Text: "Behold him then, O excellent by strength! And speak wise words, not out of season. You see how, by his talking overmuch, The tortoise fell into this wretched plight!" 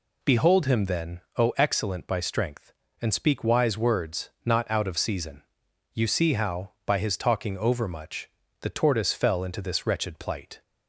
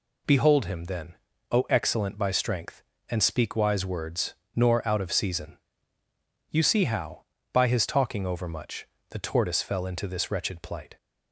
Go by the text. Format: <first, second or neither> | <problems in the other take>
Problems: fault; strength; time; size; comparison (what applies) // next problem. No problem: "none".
first | says "nor" for "not"; at 4.5 s